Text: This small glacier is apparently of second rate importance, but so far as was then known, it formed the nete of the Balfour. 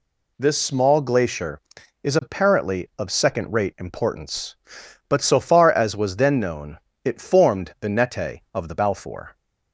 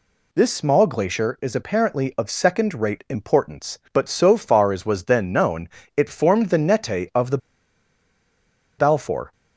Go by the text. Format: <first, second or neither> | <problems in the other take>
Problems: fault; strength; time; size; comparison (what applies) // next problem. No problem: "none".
first | pauses between "the" and "Balfour"; strong; at 7.3 s; 1.4 s long